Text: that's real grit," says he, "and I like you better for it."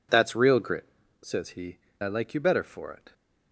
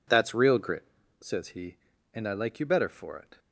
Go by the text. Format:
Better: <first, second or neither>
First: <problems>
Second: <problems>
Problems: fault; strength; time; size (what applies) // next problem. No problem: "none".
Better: second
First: skips "and"; at 1.9 s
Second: none